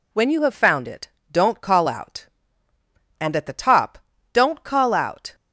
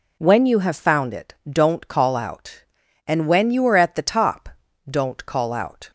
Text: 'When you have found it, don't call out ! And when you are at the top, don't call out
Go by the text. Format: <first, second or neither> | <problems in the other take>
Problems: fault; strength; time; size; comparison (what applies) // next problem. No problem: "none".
second | skips "when you are"; at 3.3 s